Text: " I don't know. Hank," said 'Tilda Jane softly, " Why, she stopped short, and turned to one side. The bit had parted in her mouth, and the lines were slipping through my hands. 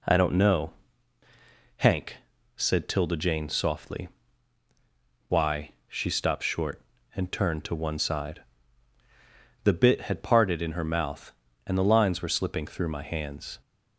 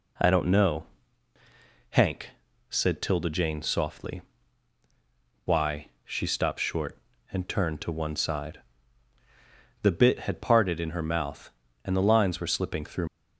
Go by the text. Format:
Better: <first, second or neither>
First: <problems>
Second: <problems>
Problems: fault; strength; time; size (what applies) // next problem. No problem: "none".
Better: first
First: none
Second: stops before "my hands"; at 13.0 s